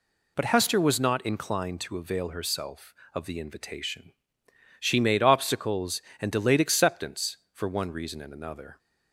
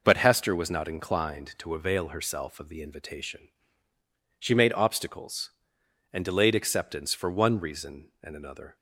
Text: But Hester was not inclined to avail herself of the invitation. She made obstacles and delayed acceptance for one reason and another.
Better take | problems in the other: neither | none

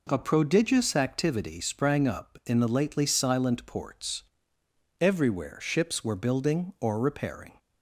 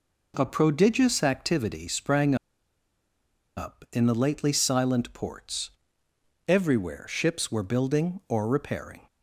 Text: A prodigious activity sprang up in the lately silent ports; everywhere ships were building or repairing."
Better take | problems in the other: first | pauses between "sprang" and "up"; at 2.3 s; 1.2 s long

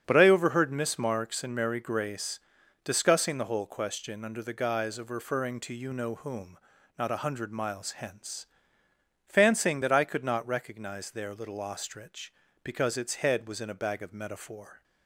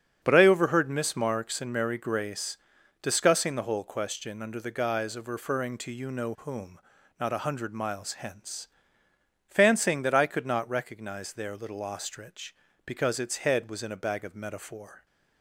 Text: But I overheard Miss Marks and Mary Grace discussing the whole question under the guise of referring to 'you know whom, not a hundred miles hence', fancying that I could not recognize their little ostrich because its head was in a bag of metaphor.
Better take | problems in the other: neither | starts louder than the rest; strong; the same in both // pauses between "Grace" and "discussing"; the same in both

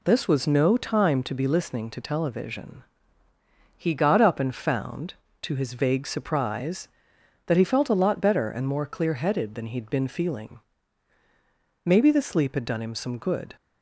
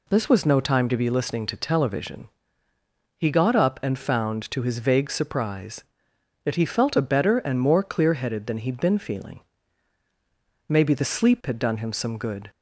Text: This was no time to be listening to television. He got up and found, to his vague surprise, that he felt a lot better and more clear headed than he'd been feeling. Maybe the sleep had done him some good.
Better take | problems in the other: first | skips "lot"; at 7.0 s

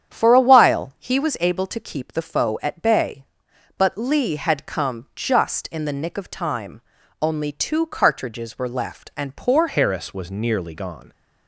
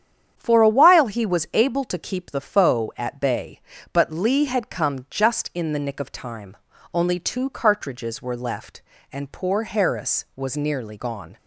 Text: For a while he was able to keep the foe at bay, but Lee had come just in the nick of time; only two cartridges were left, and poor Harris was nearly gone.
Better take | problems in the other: second | starts louder than the rest; strong; until 1.1 s; 9 dB; strong in the second // changes voice at "Harris"; from 9.6 s on; 1.5 s long

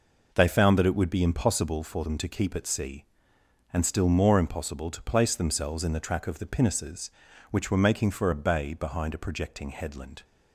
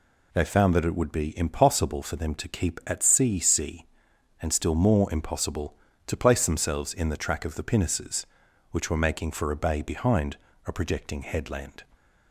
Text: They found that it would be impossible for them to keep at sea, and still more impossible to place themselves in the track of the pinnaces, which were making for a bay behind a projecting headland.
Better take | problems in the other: first | says "sea" twice; at 3.3 s // pauses between "behind" and "a"; slight; at 10.3 s; 0.28 s long

